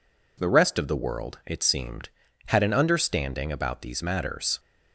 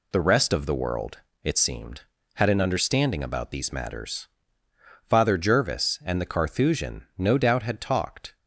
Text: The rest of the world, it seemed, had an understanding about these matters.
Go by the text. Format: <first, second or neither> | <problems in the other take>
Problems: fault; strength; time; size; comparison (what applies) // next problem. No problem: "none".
first | goes on to say "Father Jervis and the Carthusian no doubt had talked"; strong; from 5.0 s on; 3.2 s long